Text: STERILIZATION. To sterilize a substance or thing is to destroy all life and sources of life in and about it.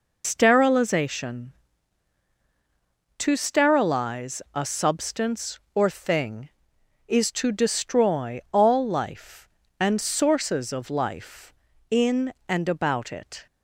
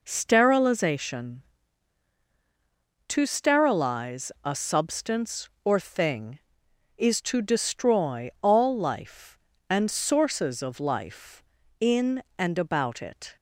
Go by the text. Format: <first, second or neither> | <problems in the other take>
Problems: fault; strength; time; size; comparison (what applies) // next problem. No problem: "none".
second | loses the start of "STERILIZATION"; at 0.2 s; 105 ms